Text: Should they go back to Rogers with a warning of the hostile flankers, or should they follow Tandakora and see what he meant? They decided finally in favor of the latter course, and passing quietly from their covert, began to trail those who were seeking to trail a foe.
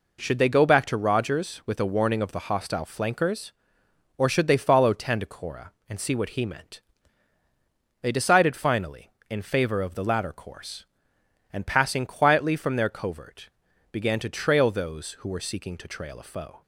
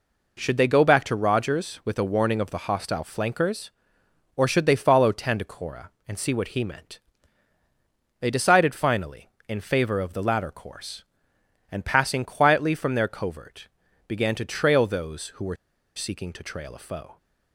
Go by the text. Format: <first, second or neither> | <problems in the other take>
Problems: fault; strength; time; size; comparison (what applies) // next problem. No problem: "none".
first | pauses between "were" and "seeking"; at 15.5 s; 0.39 s long